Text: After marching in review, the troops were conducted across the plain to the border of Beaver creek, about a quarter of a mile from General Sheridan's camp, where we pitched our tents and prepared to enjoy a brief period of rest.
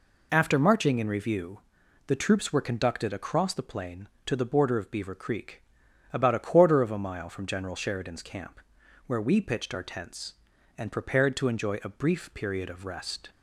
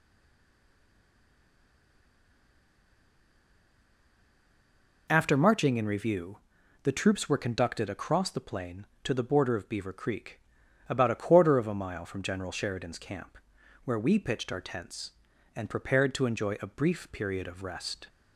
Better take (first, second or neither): first